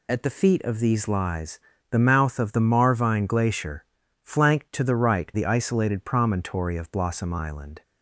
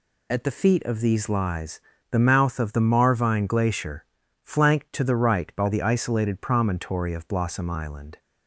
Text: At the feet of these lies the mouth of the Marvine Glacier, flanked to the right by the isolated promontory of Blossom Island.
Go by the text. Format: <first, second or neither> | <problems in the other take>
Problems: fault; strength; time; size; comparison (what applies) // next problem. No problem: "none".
second | pauses between "lies" and "the"; slight; at 1.5 s; 0.32 s long; slight in the second // skips "by"; at 5.3 s